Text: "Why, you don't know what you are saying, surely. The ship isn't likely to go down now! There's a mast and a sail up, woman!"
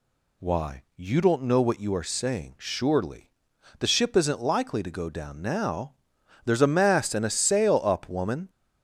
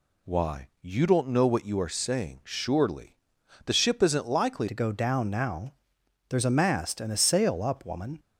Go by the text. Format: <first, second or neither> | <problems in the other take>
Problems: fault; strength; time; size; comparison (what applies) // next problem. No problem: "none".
first | changes voice at "to"; from 4.6 s on; 3.5 s long